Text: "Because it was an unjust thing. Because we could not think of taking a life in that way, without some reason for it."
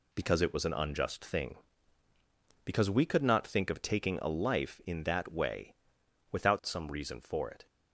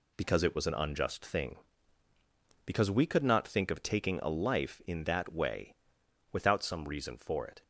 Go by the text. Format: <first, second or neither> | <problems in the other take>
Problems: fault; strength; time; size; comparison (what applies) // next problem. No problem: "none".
neither | none